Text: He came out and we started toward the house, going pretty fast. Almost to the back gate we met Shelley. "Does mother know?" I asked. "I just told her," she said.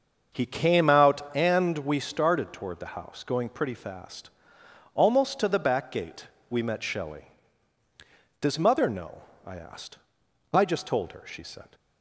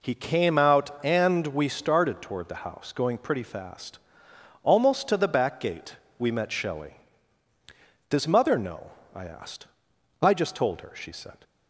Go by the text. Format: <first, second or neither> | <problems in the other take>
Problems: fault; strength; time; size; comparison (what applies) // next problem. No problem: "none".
second | starts louder than the rest; until 1.5 s; 6.5 dB // pauses between "gate" and "we"; slight; at 6.2 s; 0.24 s long; slight in the second